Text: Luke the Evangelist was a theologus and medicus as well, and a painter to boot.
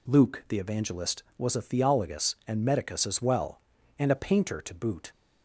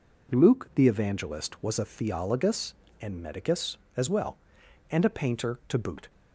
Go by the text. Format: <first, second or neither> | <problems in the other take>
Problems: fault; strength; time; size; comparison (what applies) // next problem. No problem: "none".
neither | none